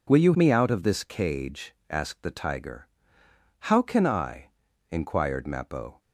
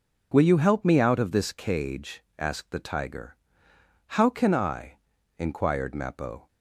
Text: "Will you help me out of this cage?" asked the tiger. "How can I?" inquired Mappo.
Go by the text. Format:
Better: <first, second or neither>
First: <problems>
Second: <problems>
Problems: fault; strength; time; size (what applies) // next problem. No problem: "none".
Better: second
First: skips "help"; at 0.3 s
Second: none